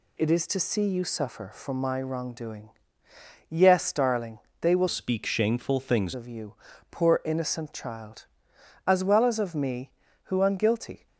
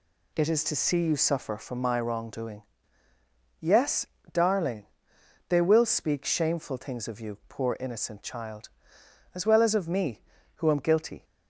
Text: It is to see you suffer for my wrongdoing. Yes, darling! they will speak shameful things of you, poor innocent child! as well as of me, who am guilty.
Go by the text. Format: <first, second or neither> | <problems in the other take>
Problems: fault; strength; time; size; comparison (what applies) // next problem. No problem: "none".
second | changes voice from "speak" to "things"; from 4.8 to 6.1 s; 1.3 s long